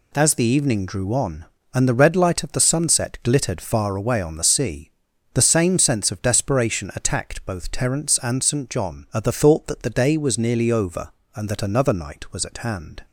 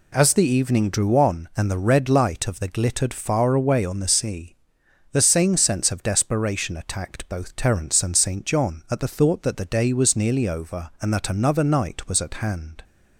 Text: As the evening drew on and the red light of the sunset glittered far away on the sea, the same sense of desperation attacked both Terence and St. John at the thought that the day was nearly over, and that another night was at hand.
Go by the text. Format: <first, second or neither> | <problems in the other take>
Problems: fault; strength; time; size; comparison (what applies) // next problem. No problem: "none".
first | skips "sunset"; at 2.6 s